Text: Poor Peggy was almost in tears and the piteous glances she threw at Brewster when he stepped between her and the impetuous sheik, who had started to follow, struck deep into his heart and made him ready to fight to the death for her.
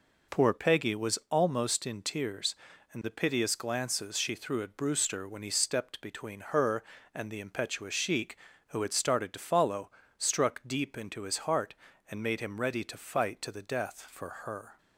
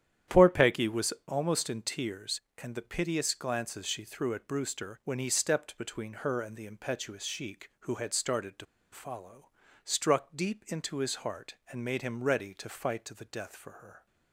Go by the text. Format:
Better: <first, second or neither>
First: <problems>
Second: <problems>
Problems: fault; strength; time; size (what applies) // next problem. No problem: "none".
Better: first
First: none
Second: starts louder than the rest; strong; until 1.4 s; 10.5 dB // pauses between "was" and "almost"; slight; at 1.1 s; 0.16 s long // pauses between "to" and "follow"; slight; at 8.6 s; 0.28 s long